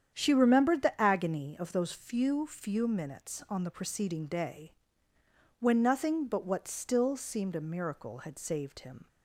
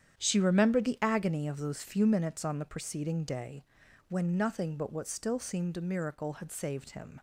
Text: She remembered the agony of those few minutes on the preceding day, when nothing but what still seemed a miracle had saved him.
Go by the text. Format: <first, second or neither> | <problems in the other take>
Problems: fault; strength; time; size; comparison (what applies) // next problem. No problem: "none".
second | starts louder than the rest; strong; until 1.1 s; 8.5 dB; strong in the second // says "few" twice; at 2.4 s